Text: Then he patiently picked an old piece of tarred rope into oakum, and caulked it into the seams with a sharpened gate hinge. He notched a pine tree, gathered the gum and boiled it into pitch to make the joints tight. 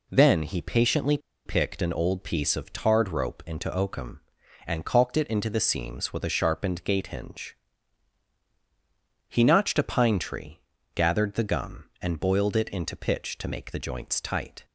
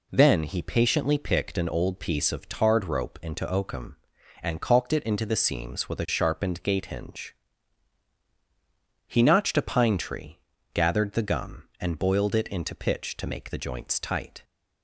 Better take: second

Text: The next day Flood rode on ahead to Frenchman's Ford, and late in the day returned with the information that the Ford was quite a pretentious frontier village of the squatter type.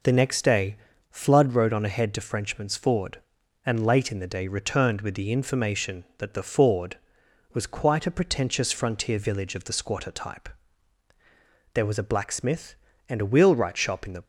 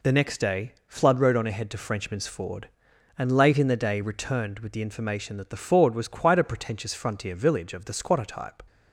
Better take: second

